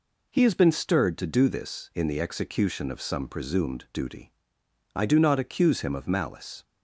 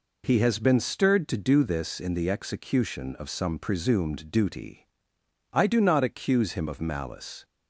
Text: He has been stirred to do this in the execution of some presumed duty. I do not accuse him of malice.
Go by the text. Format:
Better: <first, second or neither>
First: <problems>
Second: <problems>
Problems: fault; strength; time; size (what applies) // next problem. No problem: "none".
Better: neither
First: none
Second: none